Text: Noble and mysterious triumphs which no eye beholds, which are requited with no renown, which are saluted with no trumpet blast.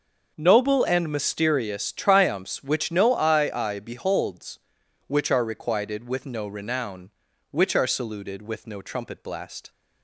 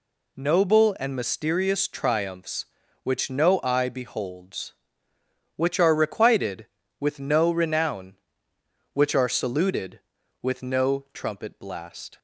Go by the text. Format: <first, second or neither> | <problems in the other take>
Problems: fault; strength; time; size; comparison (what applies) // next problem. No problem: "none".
second | starts louder than the rest; noticeable; until 1.3 s; 6 dB // says "eye" twice; at 3.5 s